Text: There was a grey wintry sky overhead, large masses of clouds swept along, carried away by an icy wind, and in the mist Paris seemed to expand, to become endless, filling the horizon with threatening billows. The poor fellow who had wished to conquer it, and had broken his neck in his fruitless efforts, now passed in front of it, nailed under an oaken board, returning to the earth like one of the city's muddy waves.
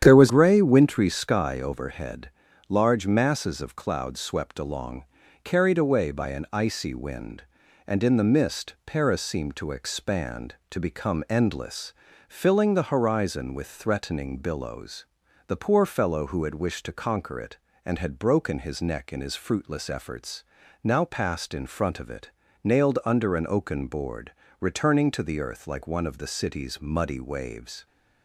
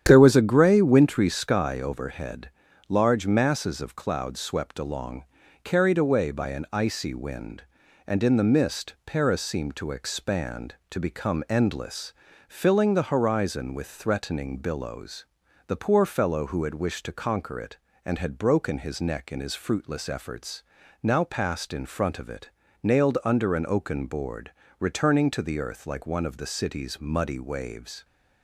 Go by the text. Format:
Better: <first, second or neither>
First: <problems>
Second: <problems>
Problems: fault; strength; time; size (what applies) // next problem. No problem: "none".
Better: second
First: starts louder than the rest; strong; until 1.0 s; 9.5 dB // skips "a"; at 0.2 s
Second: starts louder than the rest; strong; until 1.0 s; 9.5 dB